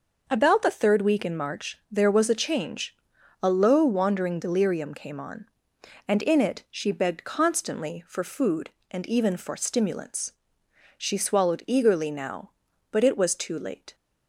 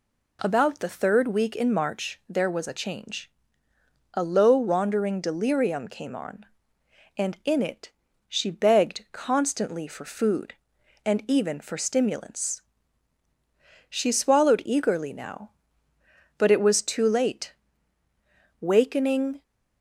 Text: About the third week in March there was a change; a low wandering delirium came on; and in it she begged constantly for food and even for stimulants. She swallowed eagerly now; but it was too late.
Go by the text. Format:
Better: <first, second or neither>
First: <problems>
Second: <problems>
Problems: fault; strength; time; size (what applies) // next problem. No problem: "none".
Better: first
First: none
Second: pauses between "it" and "she"; slight; at 7.9 s; 0.36 s long // goes on to say "Wakening"; noticeable; from 18.6 s on; 0.80 s long